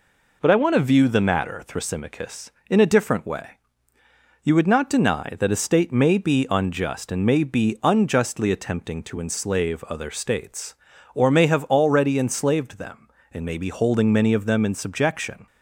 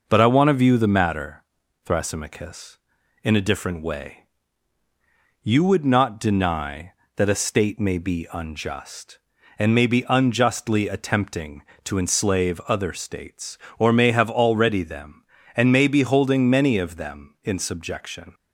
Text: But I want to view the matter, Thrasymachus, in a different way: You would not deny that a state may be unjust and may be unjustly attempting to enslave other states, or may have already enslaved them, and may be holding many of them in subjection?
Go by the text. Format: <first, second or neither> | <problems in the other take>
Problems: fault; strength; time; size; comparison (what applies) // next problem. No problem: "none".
first | skips "enslaved"; at 14.8 s